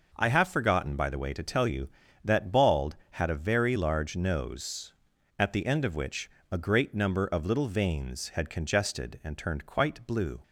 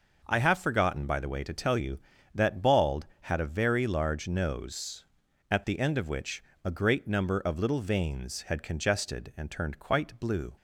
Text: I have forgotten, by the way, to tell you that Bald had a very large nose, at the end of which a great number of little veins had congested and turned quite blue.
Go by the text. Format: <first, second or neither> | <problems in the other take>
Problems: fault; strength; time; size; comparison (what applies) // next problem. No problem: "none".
neither | pauses between "which" and "a"; slight; the same in both